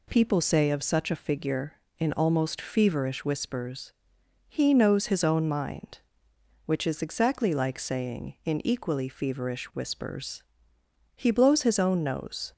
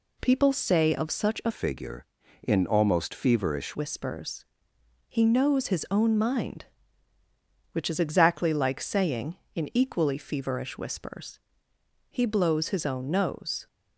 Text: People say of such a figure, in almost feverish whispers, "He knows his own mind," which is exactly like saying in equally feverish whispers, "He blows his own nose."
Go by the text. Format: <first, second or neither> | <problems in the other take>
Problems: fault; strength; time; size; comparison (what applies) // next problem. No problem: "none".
first | changes voice from "figure" to "feverish"; from 1.5 to 3.7 s; 2.2 s long